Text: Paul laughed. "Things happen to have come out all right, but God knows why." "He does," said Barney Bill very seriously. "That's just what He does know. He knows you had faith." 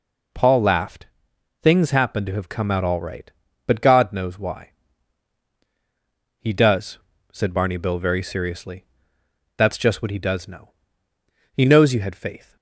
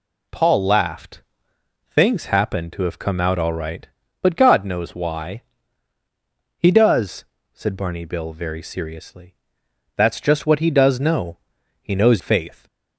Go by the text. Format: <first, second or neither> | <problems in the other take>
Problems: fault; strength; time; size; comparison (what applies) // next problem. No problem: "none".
first | skips "you had"; at 12.2 s